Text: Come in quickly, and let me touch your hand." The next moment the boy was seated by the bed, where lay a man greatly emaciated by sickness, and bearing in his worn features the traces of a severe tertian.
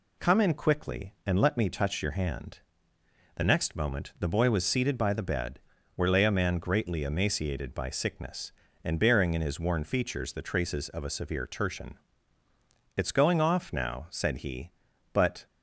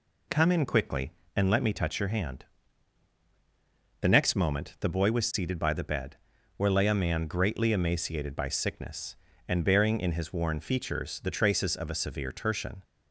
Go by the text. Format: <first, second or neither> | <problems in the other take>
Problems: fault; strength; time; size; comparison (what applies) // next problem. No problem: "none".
second | goes on to say "It's going off now said he but"; strong; from 12.9 s on; 2.5 s long